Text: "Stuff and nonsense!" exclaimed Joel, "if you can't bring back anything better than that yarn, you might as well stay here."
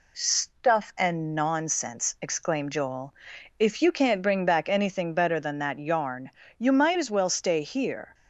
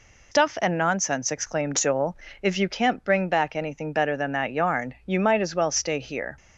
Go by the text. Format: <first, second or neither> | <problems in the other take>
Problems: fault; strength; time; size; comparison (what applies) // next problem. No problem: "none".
first | loses the start of "Stuff"; at 0.3 s; 170 ms